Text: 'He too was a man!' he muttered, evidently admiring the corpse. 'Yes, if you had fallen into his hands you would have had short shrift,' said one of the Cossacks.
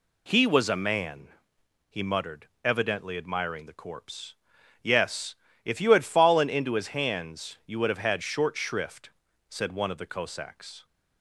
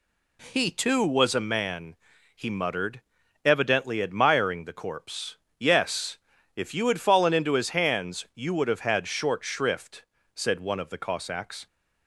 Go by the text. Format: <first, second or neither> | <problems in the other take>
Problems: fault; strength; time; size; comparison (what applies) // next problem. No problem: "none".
second | skips "too"; at 0.4 s